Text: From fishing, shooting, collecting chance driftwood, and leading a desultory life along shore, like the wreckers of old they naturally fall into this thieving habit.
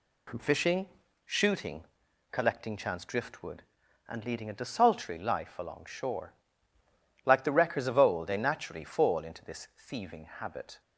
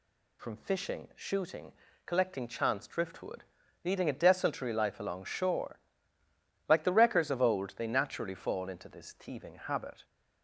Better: first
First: none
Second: skips "and"; at 3.6 s

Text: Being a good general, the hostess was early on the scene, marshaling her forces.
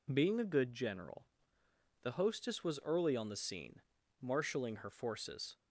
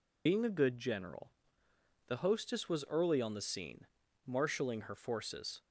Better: first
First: none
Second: loses the start of "Being"; at 0.2 s; 130 ms

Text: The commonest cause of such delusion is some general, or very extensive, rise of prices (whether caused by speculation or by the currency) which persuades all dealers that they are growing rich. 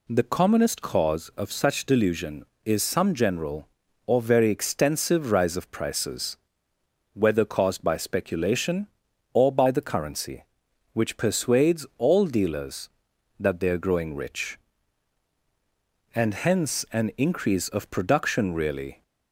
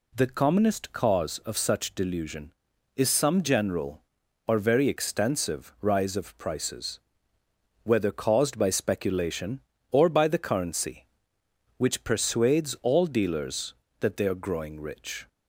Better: second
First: goes on to say "And hence an increase of production really"; strong; from 16.1 s on; 2.8 s long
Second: none

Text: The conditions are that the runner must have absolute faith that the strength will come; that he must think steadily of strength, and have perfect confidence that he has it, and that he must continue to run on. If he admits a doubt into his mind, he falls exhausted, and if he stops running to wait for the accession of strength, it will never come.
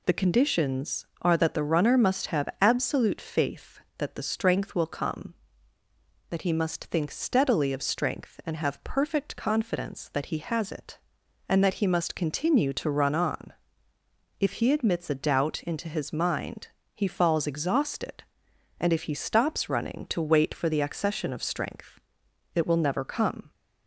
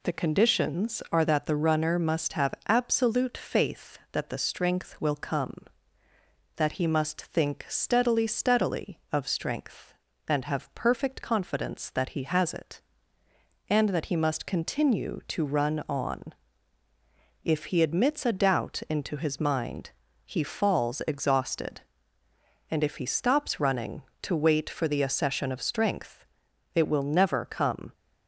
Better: first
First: none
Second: says "steadily" twice; at 8.2 s

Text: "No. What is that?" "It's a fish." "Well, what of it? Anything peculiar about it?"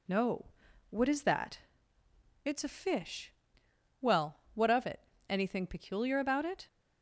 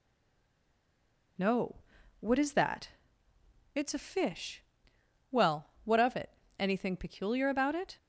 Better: first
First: none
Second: stays silent before the first word; noticeable; until 1.3 s; 1.3 s long

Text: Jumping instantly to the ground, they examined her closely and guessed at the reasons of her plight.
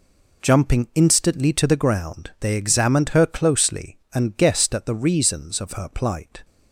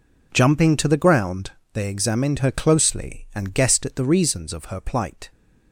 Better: first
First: none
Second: skips "instantly"; at 0.7 s

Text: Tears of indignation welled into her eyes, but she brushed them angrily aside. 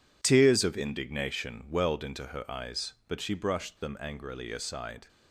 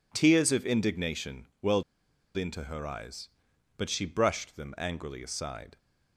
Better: first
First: none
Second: pauses between "welled" and "into"; noticeable; at 1.8 s; 0.52 s long

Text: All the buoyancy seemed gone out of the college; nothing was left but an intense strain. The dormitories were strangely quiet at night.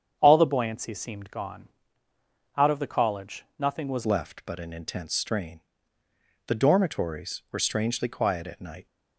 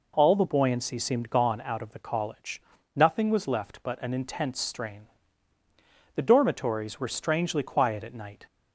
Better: second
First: starts louder than the rest; strong; until 1.2 s; 8 dB // pauses between "gone" and "out"; noticeable; at 1.6 s; 0.88 s long // changes voice at "left"; from 4.0 s on; 4.8 s long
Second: none

